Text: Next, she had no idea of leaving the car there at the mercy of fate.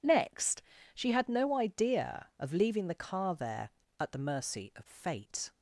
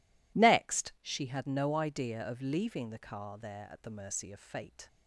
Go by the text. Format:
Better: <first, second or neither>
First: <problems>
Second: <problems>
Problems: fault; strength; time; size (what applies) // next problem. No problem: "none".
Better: neither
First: none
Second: none